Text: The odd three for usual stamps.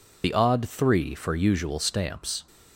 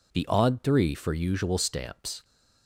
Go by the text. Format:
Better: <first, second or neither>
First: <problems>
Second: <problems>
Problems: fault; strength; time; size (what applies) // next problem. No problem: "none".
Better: second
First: loses the start of "The"; at 0.2 s; 35 ms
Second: none